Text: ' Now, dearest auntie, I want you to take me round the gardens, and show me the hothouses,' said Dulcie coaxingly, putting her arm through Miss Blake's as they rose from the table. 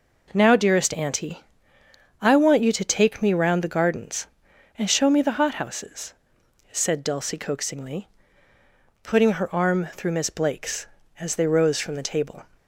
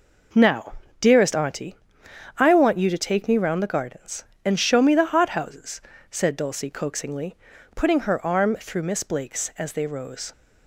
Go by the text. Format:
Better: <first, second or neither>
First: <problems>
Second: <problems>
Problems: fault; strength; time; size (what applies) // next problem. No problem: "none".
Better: first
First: none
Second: stops before "from the table"; at 10.3 s